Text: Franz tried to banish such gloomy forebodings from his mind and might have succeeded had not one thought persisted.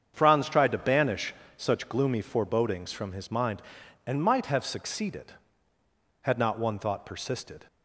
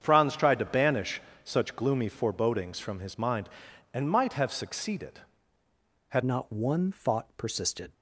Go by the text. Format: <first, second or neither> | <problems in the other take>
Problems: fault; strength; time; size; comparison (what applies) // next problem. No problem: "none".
first | starts louder than the rest; strong; until 1.0 s; 8 dB; strong in the first // pauses between "banish" and "such"; slight; at 1.2 s; 0.22 s long; slight in the first // changes voice at "not"; from 6.2 s on; 1.7 s long